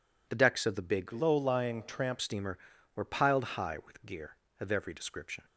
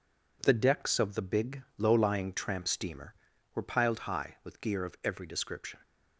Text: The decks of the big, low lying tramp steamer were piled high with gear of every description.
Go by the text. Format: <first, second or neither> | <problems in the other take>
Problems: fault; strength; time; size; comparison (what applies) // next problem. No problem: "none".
second | changes voice from "low" to "tramp"; from 1.1 to 2.1 s; 1.0 s long